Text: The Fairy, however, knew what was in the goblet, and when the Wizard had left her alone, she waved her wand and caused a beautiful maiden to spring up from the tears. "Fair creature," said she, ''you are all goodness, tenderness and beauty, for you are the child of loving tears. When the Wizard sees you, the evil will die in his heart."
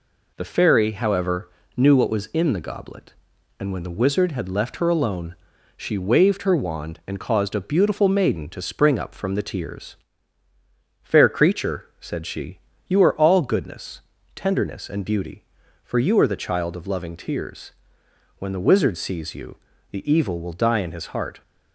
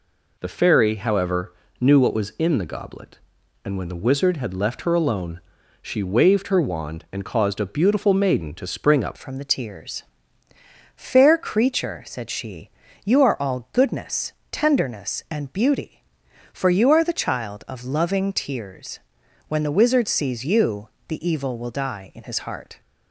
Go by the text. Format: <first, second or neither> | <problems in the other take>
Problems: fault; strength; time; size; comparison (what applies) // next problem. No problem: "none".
first | changes voice at "from"; from 9.1 s on; 13.7 s long